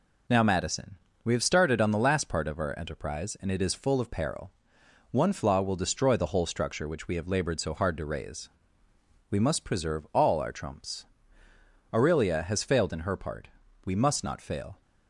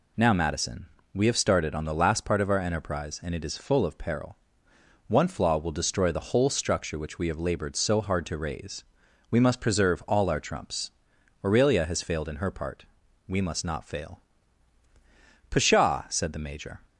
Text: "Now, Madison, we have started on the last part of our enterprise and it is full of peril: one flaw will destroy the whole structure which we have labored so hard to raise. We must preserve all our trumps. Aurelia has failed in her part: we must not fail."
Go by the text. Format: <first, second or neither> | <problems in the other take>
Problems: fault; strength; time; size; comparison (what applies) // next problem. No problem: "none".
first | goes on to say "Pshaw said the Major"; from 15.4 s on; 1.3 s long